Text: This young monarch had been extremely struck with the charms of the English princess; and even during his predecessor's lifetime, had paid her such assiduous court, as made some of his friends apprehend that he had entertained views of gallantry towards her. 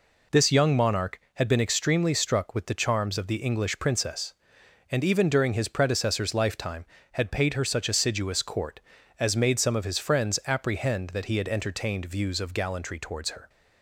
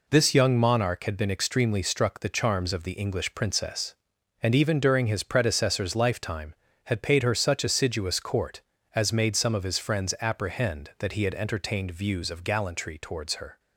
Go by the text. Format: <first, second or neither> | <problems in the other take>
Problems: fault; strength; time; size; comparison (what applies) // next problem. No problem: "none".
first | skips "with"; at 2.2 s